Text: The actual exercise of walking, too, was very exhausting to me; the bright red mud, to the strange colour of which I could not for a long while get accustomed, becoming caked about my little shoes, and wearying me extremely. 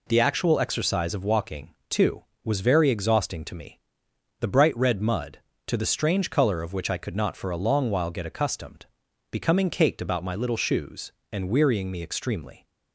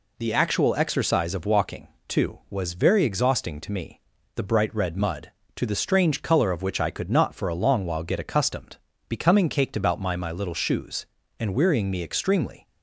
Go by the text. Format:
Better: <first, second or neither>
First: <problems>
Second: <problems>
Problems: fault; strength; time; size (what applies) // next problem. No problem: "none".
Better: first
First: none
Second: says "my" twice; at 10.1 s